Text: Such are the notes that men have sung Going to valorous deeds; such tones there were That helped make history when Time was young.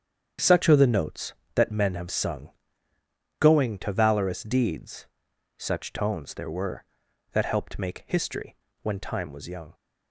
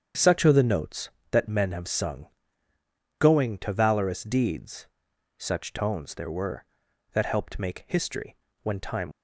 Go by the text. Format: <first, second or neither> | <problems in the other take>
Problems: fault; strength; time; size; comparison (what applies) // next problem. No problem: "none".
first | starts louder than the rest; strong; until 1.3 s; 8 dB; strong in the first // pauses between "sung" and "Going"; noticeable; at 2.2 s; 0.92 s long; noticeable in the first // pauses between "history" and "when"; slight; at 8.3 s; 0.28 s long; slight in the first // stops before "was young"; at 9.1 s